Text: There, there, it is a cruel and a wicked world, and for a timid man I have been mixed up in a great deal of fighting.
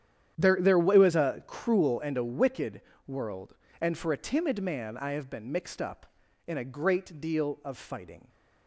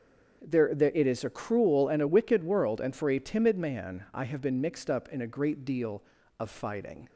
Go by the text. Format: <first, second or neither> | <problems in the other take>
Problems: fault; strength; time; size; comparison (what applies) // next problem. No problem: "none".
second | starts louder than the rest; strong; until 1.4 s; 9.5 dB; also in the second // says "was" for "is"; at 0.9 s // pauses between "wicked" and "world"; slight; at 2.8 s; 0.26 s long